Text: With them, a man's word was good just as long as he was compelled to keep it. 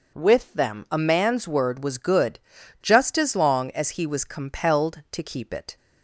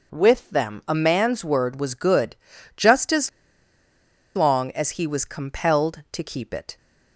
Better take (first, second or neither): first